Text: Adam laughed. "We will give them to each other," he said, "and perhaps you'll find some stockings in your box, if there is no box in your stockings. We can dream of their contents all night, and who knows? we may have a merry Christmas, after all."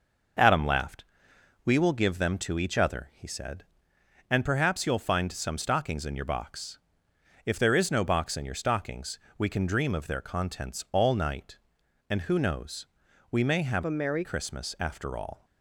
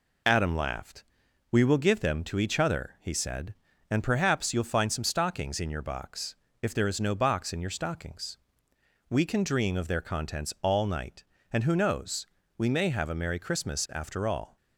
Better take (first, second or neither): second